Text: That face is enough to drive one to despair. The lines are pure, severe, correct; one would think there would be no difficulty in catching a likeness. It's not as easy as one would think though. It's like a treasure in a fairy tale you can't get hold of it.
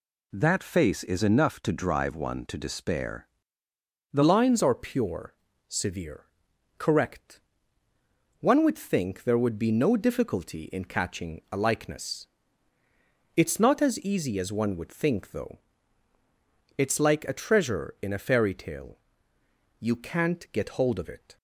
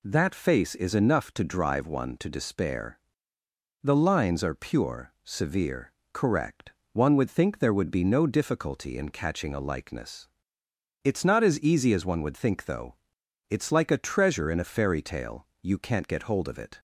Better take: second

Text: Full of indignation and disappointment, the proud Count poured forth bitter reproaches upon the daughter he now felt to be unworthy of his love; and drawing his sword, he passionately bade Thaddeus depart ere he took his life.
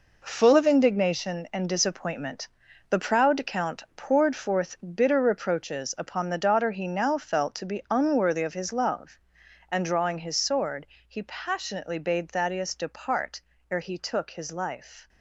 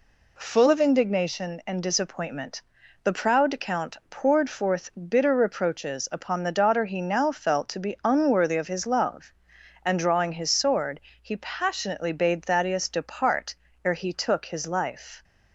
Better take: second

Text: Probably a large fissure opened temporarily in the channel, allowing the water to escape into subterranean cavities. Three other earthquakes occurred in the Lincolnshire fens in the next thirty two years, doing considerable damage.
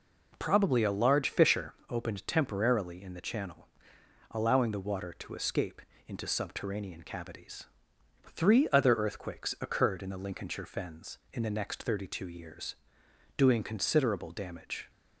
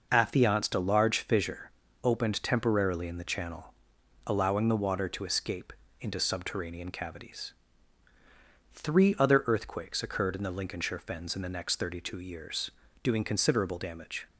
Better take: first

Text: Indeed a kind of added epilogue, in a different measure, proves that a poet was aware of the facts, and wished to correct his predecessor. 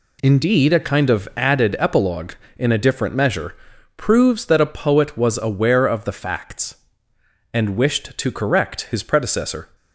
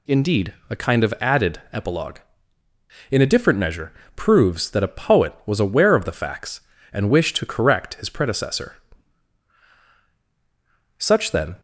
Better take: first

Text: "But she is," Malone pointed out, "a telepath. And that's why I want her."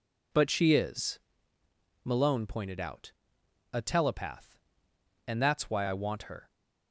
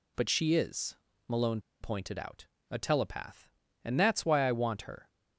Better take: first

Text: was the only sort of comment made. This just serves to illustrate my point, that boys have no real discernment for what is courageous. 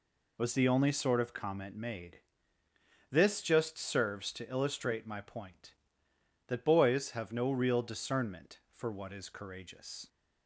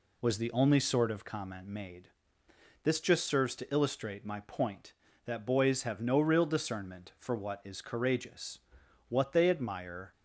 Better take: first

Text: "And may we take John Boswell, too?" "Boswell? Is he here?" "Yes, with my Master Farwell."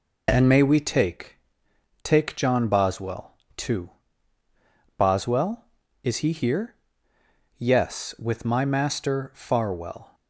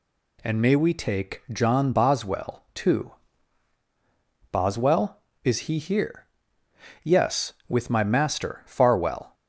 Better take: second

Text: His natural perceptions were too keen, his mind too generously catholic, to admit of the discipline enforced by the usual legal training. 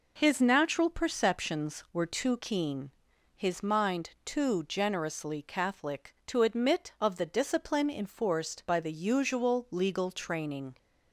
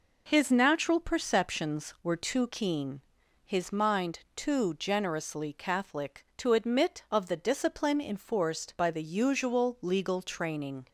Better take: neither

